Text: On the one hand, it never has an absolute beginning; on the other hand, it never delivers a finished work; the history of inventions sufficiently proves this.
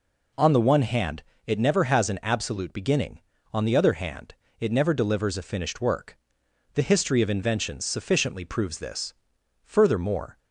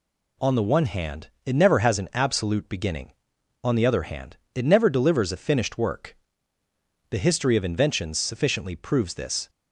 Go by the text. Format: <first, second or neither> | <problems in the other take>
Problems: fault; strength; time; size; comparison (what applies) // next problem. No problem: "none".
second | goes on to say "Furthermore"; noticeable; from 9.6 s on; 0.76 s long